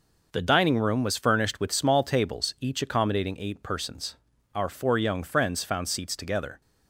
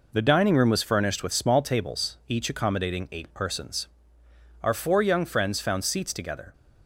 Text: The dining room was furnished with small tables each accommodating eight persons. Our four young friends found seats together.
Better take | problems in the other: neither | none

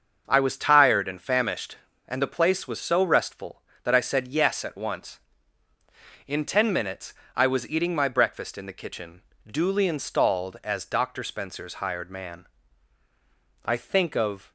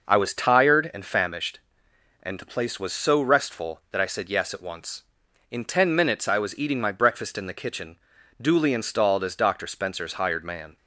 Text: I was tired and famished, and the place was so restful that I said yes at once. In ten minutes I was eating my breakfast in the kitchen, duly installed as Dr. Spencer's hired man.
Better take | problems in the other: second | starts louder than the rest; until 1.2 s; 6.5 dB // pauses between "minutes" and "I"; slight; at 7.1 s; 0.22 s long // goes on to say "I think of"; noticeable; from 13.6 s on; 0.86 s long

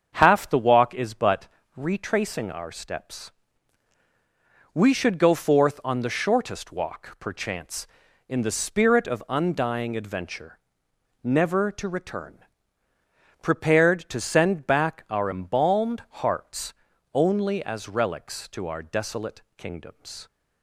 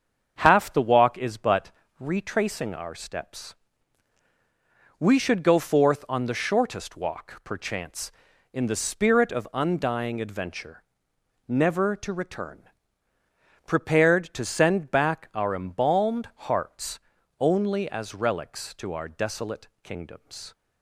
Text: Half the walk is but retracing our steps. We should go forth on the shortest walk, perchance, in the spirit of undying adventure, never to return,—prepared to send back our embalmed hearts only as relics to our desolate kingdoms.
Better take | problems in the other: neither | starts louder than the rest; strong; the same in both // pauses between "but" and "retracing"; slight; the same in both // pauses between "hearts" and "only"; the same in both

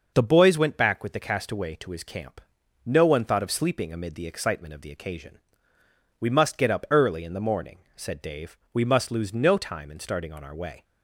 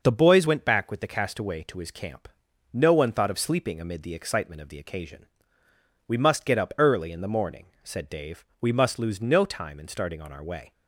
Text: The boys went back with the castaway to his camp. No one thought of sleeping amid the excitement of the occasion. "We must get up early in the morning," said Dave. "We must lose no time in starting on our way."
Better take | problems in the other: neither | none

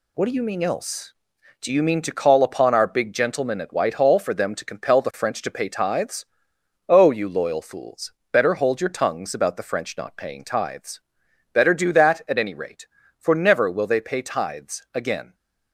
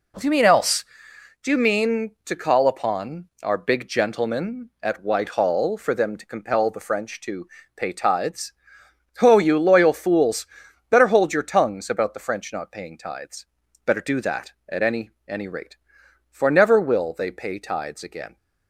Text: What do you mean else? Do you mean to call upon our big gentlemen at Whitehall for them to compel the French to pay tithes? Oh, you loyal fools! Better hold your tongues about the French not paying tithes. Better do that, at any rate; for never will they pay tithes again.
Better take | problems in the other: first | pauses between "upon" and "our"; slight; at 3.2 s; 0.18 s long // pauses between "to" and "pay"; slight; at 7.4 s; 0.26 s long // says "any" twice; at 15.2 s

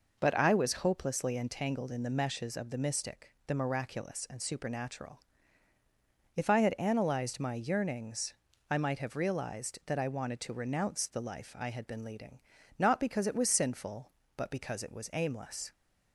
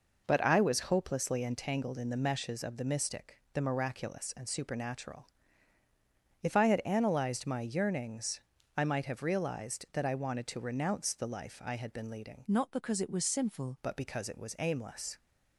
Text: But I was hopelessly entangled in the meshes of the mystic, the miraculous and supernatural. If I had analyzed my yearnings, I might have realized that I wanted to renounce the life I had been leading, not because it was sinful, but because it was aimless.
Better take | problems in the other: first | changes voice from "not" to "sinful"; from 12.4 to 13.7 s; 1.3 s long

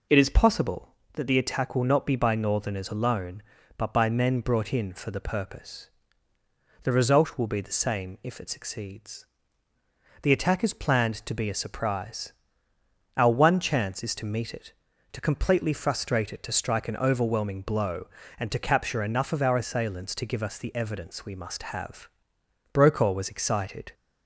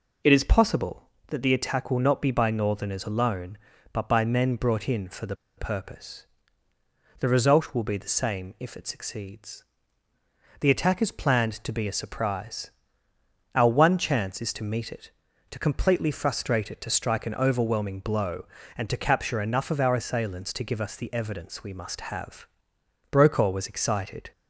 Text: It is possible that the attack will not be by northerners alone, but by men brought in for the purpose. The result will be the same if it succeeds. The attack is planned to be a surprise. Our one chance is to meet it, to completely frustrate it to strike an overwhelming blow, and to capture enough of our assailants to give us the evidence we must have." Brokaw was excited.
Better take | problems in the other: first | pauses between "the" and "purpose"; slight; at 5.3 s; 0.21 s long

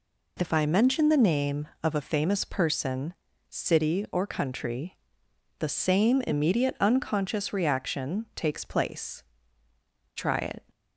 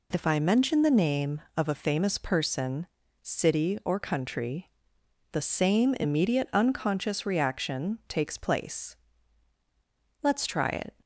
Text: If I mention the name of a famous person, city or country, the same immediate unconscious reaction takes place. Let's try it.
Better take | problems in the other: second | skips "Let's"; at 9.6 s

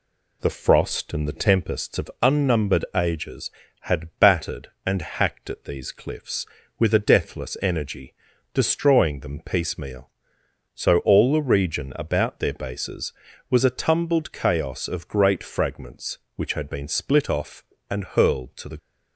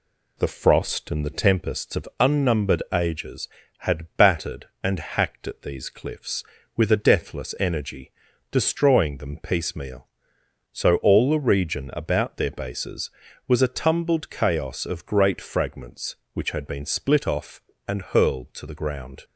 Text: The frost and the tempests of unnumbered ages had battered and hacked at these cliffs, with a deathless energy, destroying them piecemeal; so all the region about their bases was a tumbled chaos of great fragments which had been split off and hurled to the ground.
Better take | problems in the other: second | stops before "ground"; at 18.7 s

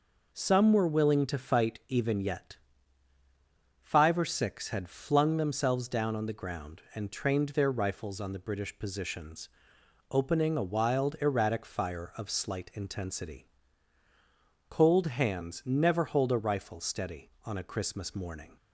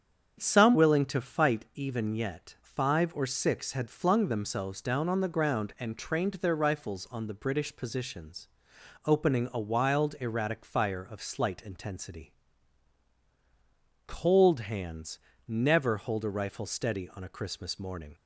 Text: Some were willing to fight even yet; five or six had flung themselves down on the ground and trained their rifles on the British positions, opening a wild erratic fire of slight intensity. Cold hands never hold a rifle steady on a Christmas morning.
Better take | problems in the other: first | starts louder than the rest; strong; until 1.4 s; 7.5 dB // skips "were"; at 0.7 s // pauses between "hands" and "never"; slight; at 15.1 s; 0.30 s long

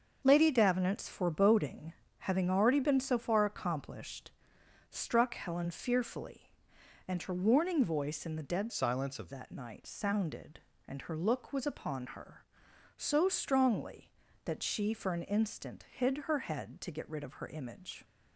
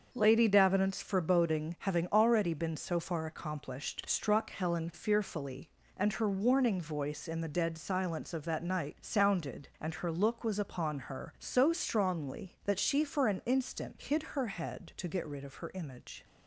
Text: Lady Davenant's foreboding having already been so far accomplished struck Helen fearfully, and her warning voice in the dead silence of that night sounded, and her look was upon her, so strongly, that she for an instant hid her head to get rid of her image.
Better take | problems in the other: second | starts louder than the rest; until 1.2 s; 6.5 dB; also in the second // pauses between "foreboding" and "having"; slight; at 1.9 s; 0.26 s long // pauses between "accomplished" and "struck"; noticeable; at 4.3 s; 0.58 s long // changes voice from "silence" to "of"; from 8.7 to 9.3 s; 0.6 s long

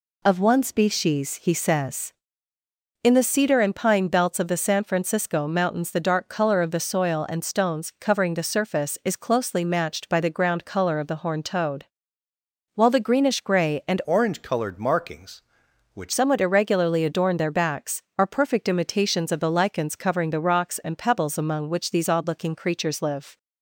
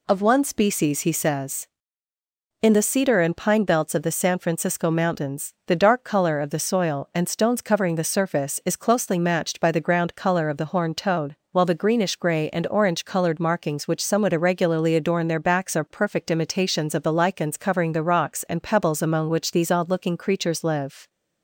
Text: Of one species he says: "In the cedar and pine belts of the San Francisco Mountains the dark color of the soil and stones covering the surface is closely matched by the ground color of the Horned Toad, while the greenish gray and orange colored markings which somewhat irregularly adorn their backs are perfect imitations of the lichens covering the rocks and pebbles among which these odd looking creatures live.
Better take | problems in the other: second | changes voice from "orange" to "which"; from 14.0 to 16.1 s; 2.1 s long

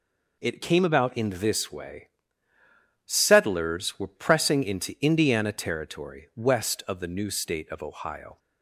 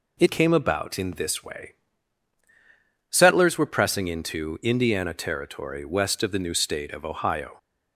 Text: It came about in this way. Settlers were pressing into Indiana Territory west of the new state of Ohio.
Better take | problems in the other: neither | none

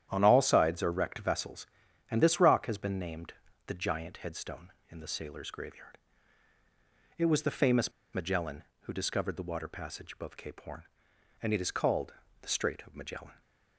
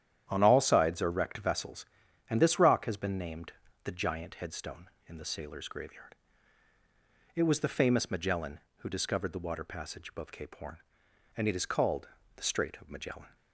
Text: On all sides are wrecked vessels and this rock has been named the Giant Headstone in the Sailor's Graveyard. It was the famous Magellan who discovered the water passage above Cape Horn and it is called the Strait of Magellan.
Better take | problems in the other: second | starts louder than the rest; strong; until 1.1 s; 10.5 dB; strong in the second // pauses between "named" and "the"; slight; at 3.3 s; 0.34 s long; slight in the second // pauses between "famous" and "Magellan"; slight; at 7.9 s; 0.22 s long // pauses between "called" and "the"; slight; at 12.1 s; 0.30 s long; slight in the second

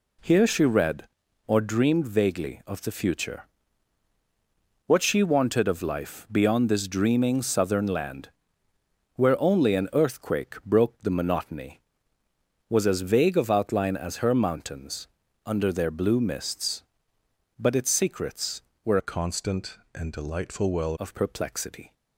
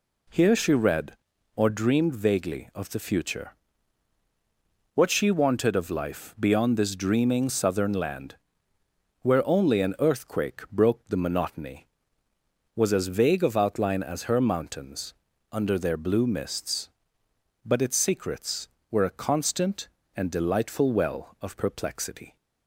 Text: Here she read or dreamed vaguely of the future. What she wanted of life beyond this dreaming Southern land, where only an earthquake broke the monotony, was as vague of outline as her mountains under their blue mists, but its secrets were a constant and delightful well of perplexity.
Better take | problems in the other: second | pauses between "mountains" and "under"; at 15.0 s; 0.38 s long; also in the second // changes voice from "a" to "well"; from 18.9 to 20.9 s; 2.0 s long

